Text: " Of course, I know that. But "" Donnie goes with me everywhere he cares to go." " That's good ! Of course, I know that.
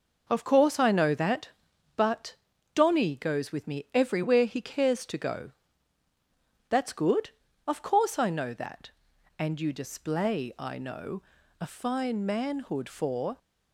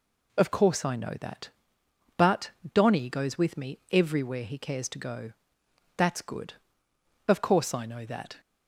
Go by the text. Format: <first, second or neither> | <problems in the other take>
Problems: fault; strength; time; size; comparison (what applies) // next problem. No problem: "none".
second | goes on to say "And you display I know a fine manhood for"; strong; from 9.3 s on; 3.9 s long